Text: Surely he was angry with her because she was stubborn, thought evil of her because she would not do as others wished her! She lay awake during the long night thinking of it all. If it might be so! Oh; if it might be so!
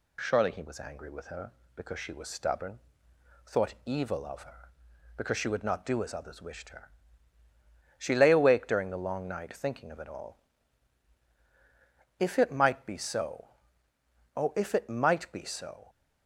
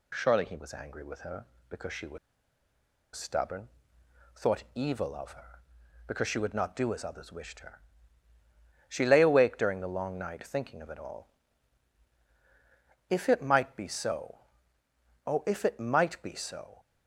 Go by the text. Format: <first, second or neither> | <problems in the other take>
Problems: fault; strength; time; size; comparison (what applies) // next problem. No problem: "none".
first | pauses between "was" and "stubborn"; noticeable; at 2.1 s; 0.97 s long